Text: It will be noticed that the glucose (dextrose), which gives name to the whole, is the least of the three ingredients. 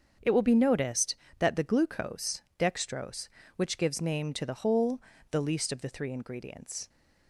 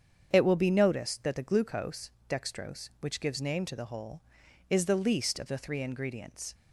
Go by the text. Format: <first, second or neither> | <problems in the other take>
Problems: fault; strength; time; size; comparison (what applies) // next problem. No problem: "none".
second | starts louder than the rest; until 1.4 s; 7 dB; strong in the second // skips "is"; at 5.1 s